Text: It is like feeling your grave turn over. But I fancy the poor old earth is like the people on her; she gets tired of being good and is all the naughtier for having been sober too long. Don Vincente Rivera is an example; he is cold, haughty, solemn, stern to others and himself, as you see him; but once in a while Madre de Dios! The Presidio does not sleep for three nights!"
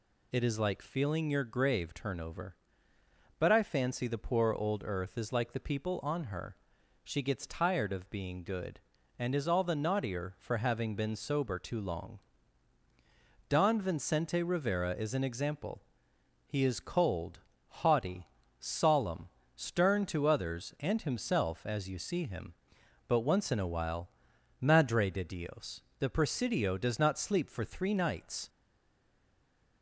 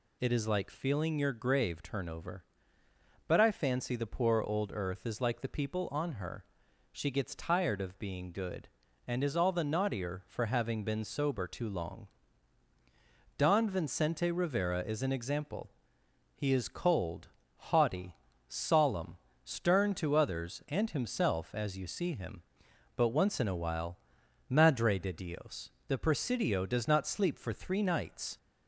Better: second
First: pauses between "while" and "Madre"; noticeable; at 24.0 s; 0.52 s long // stays silent after the last word; noticeable; from 28.4 s on; 1.4 s long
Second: pauses between "while" and "Madre"; noticeable; at 23.9 s; 0.52 s long

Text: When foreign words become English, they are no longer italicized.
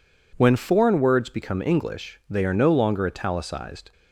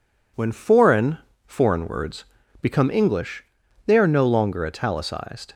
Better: first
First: none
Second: says "foreign" twice; at 1.4 s // pauses between "words" and "become"; slight; at 2.2 s; 0.36 s long

